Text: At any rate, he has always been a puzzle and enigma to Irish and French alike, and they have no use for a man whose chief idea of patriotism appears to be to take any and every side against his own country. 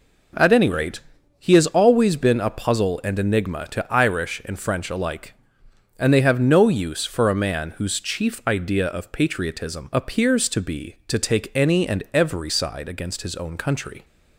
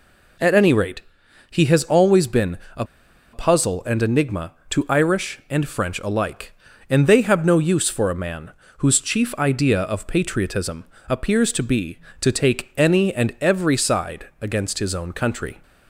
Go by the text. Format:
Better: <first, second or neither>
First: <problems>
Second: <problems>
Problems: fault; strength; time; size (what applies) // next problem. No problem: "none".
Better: first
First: none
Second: pauses between "been" and "a"; slight; at 2.5 s; 0.18 s long // pauses between "a" and "puzzle"; noticeable; at 2.8 s; 0.49 s long // pauses between "man" and "whose"; slight; at 8.4 s; 0.28 s long // pauses between "patriotism" and "appears"; slight; at 10.8 s; 0.24 s long